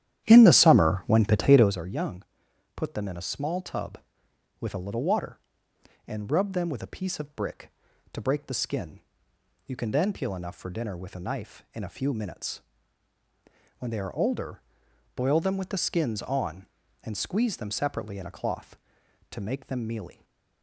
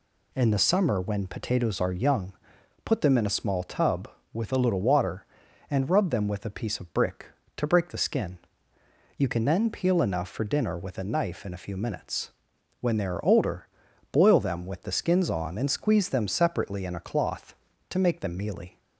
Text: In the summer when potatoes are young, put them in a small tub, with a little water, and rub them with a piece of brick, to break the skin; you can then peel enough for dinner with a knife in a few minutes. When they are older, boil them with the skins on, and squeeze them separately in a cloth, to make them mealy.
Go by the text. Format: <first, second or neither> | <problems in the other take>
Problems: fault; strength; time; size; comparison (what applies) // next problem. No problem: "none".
second | starts louder than the rest; strong; until 1.8 s; 11 dB // stays silent after the last word; slight; from 20.1 s on; 0.5 s long